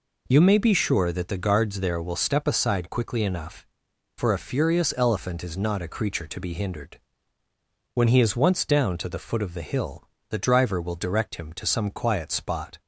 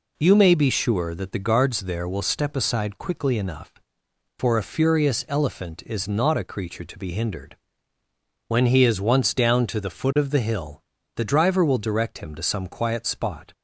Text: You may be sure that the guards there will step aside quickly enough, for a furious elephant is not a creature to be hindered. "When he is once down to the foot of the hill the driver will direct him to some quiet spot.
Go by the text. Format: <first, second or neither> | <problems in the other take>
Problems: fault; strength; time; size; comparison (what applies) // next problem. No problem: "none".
neither | pauses between "hill" and "the"; slight; the same in both